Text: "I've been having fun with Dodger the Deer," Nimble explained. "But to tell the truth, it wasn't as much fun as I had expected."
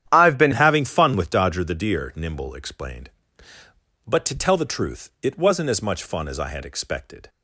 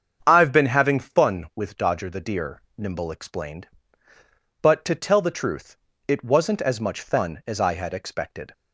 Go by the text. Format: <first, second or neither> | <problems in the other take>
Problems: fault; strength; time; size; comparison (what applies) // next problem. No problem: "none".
second | starts louder than the rest; strong; until 1.1 s; 10 dB; strong in the second // changes voice at "having"; from 0.5 s on; 6.7 s long